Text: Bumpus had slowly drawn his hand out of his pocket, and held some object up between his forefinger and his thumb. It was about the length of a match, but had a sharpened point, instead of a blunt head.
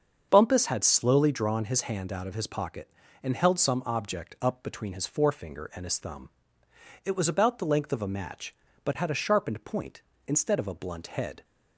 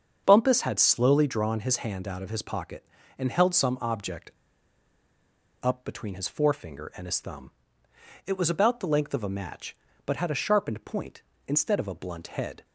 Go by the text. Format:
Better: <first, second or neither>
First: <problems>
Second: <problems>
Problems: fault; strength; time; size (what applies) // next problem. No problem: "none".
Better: first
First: starts louder than the rest; until 1.3 s; 7 dB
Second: starts louder than the rest; until 1.2 s; 7 dB // pauses between "object" and "up"; strong; at 4.3 s; 1.3 s long